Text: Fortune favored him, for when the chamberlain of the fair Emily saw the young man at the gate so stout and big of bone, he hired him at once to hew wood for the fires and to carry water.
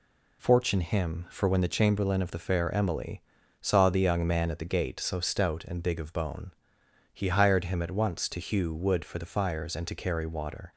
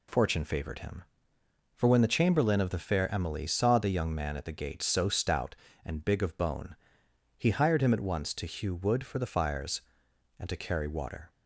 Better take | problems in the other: second | skips "favored"; at 0.8 s // pauses between "Emily" and "saw"; at 3.2 s; 0.39 s long

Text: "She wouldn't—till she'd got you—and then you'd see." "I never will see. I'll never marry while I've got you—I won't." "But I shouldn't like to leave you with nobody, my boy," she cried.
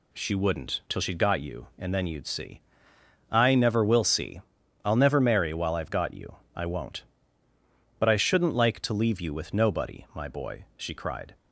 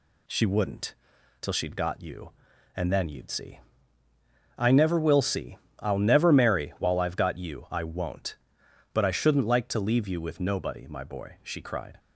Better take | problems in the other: neither | none

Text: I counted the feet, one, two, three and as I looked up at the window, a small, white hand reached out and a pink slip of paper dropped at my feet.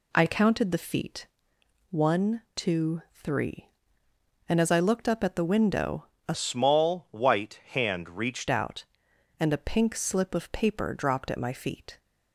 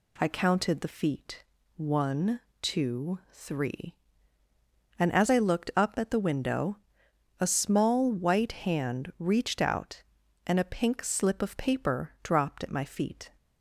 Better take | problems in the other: second | changes voice from "small" to "reached"; from 6.3 to 8.4 s; 2.1 s long

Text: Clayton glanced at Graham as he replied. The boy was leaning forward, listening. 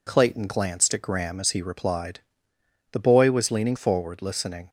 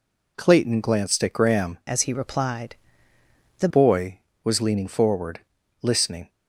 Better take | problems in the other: first | changes voice from "as" to "The"; from 1.8 to 3.6 s; 1.8 s long

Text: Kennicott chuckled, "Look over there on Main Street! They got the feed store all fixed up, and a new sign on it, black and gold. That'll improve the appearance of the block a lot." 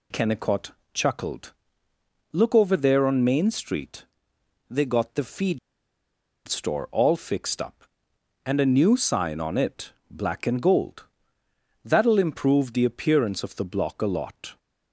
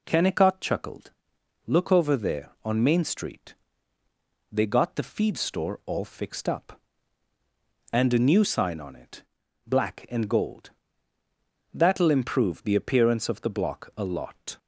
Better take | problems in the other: second | pauses between "Kennicott" and "chuckled"; slight; at 0.7 s; 0.22 s long // pauses between "feed" and "store"; noticeable; at 5.5 s; 0.89 s long

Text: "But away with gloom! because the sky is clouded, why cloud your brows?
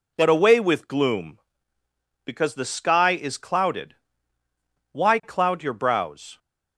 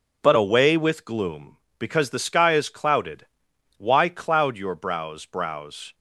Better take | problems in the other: first | says "brows" twice; at 5.2 s

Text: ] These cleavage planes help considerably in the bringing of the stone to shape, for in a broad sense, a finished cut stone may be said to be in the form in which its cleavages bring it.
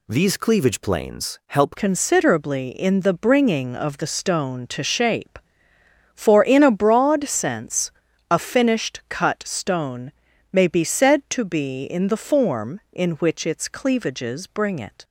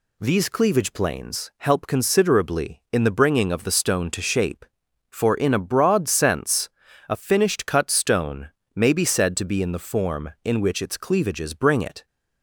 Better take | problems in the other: second | changes voice at "considerably"; from 1.7 s on; 13.3 s long // pauses between "stone" and "may"; at 10.1 s; 0.38 s long; slight in the second

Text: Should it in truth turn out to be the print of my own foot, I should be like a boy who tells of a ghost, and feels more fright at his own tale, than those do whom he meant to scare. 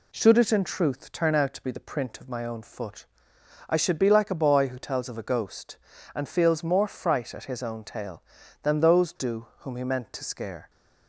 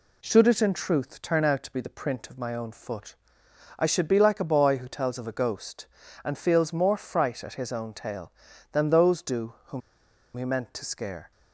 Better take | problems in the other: first | pauses between "whom" and "he"; noticeable; at 9.8 s; 0.54 s long

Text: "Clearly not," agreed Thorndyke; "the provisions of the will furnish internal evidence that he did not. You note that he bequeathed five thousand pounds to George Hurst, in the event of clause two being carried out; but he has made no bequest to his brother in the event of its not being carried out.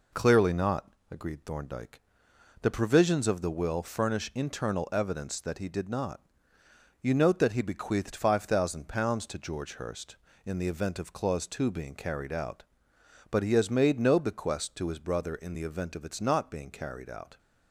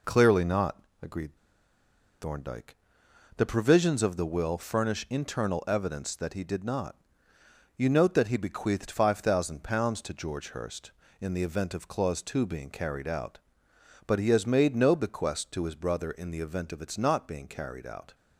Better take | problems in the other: first | pauses between "agreed" and "Thorndyke"; noticeable; at 1.3 s; 0.86 s long

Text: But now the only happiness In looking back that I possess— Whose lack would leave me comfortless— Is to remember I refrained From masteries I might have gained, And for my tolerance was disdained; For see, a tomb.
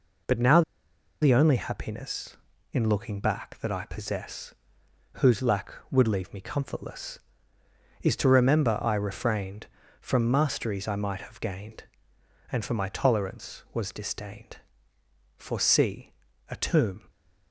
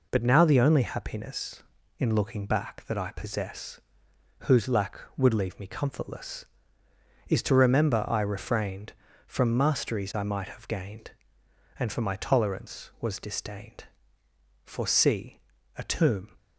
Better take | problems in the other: second | pauses between "now" and "the"; noticeable; at 0.6 s; 0.60 s long

